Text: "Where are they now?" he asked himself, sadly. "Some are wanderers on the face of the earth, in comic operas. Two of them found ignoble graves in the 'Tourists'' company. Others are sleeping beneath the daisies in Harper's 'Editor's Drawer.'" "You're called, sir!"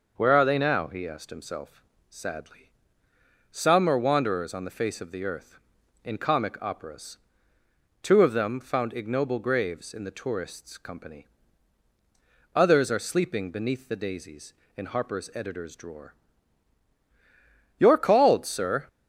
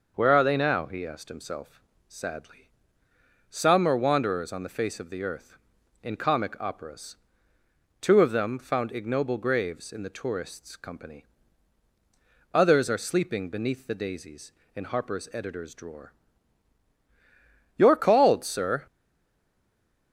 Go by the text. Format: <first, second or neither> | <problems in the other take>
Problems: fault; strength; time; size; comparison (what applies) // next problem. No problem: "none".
first | stays silent after the last word; noticeable; from 18.8 s on; 1.3 s long